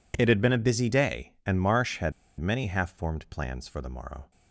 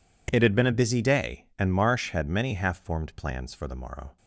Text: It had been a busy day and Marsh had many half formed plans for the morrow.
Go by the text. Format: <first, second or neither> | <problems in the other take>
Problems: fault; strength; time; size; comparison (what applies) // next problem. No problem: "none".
second | pauses between "had" and "many"; slight; at 2.1 s; 0.28 s long